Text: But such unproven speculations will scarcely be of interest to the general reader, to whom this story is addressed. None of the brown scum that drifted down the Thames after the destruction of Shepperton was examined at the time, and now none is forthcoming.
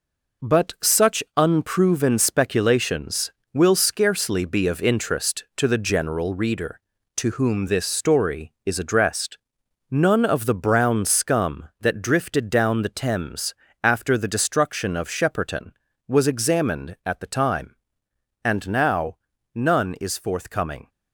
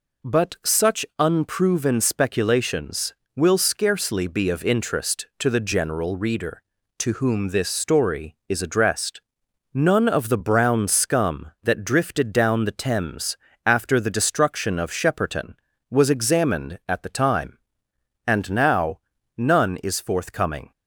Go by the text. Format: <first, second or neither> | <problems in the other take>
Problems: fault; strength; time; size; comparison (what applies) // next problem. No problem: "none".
second | gets quieter; strong; throughout; 7.5 dB // pauses between "Thames" and "after"; slight; at 13.5 s; 0.28 s long; slight in the second // pauses between "now" and "none"; at 19.1 s; 0.38 s long; also in the second